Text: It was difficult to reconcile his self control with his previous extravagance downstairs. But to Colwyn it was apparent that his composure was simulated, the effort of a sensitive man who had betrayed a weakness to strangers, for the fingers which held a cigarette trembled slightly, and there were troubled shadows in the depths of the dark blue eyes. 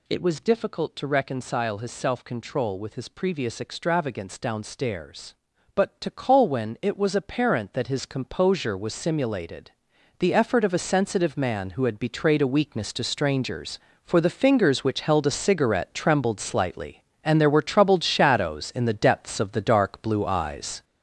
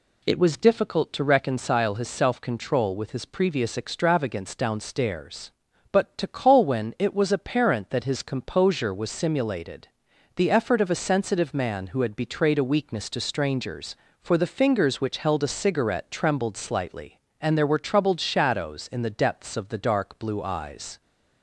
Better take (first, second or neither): second